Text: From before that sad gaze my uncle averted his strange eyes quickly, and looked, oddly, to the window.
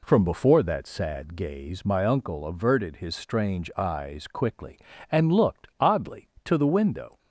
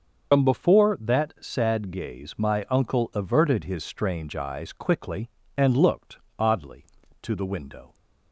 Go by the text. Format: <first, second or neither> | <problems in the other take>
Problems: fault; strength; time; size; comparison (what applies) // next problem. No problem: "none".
first | loses the start of "From"; at 0.3 s; 90 ms // starts louder than the rest; until 1.4 s; 6.5 dB